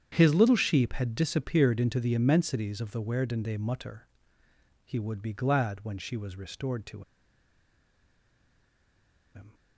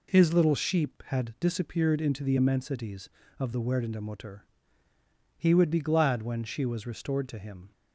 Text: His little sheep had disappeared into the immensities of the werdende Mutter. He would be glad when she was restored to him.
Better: second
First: starts louder than the rest; strong; until 1.1 s; 8.5 dB // pauses between "to" and "him"; strong; at 7.0 s; 2.3 s long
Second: none

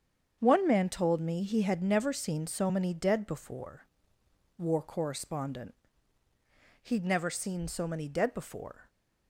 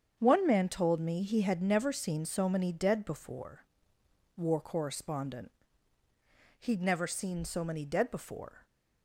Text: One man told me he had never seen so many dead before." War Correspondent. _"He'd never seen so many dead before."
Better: neither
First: starts louder than the rest; strong; until 1.4 s; 7.5 dB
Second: starts louder than the rest; strong; until 1.2 s; 7.5 dB

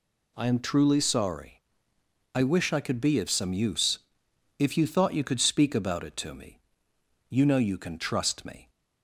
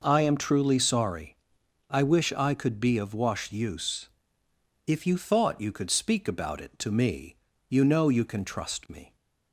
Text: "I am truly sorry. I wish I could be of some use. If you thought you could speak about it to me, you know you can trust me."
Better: first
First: none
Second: says "wash" for "some"; at 3.1 s

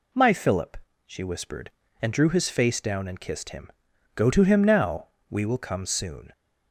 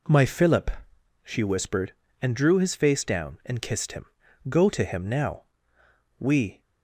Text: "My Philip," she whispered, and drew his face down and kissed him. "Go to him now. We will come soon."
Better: first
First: none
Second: stops before "will come soon"; at 6.6 s

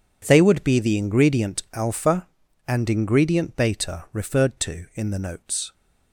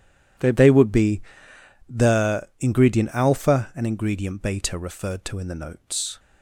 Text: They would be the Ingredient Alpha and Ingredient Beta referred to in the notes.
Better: first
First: none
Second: says "They" twice; at 0.5 s // pauses between "be" and "the"; noticeable; at 1.2 s; 0.68 s long

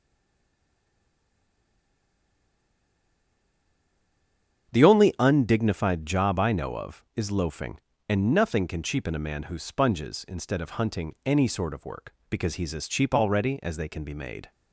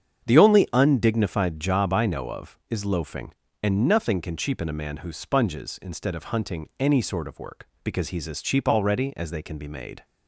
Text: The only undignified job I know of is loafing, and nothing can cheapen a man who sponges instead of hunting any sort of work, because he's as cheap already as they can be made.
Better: second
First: stays silent before the first word; strong; until 4.7 s; 4.7 s long // starts louder than the rest; strong; until 5.7 s; 8 dB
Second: starts louder than the rest; strong; until 1.2 s; 8 dB

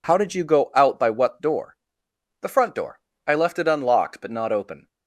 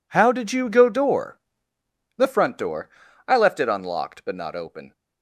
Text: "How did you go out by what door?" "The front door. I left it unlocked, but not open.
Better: first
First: none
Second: skips "out by what"; at 0.8 s

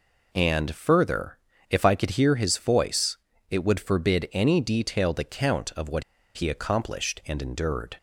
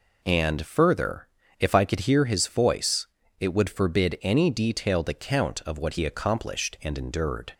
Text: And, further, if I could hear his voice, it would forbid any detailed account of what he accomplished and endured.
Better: second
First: pauses between "what" and "he"; slight; at 6.0 s; 0.34 s long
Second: none

